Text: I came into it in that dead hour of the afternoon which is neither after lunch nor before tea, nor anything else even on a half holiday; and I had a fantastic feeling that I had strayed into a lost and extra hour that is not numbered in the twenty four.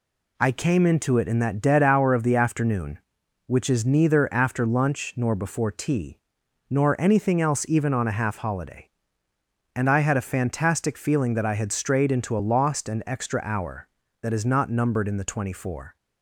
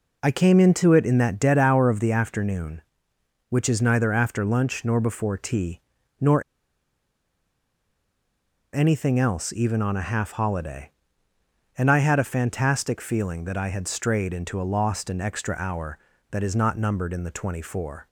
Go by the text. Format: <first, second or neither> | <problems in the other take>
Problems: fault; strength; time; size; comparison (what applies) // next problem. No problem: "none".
first | pauses between "nor" and "anything"; strong; at 6.4 s; 2.3 s long